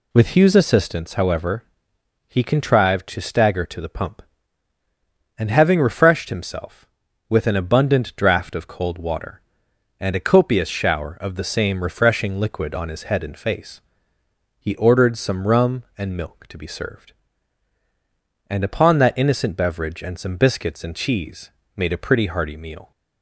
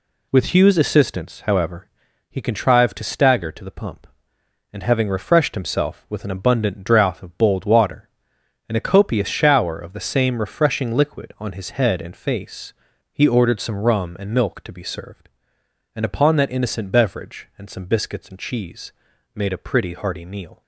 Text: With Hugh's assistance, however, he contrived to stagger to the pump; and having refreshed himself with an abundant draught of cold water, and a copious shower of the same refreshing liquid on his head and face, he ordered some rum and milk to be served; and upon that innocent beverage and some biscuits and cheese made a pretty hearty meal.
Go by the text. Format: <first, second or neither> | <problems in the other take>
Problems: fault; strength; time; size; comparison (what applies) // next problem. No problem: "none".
first | says "bold" for "cold"; at 7.3 s // pauses between "cheese" and "made"; at 18.9 s; 0.42 s long; slight in the first